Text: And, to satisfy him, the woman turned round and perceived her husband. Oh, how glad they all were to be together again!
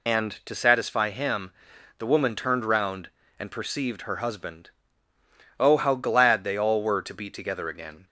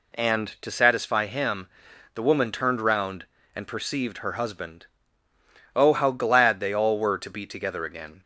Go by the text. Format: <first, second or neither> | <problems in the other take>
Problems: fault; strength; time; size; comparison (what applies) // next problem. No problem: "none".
second | loses the start of "And"; at 0.0 s; 80 ms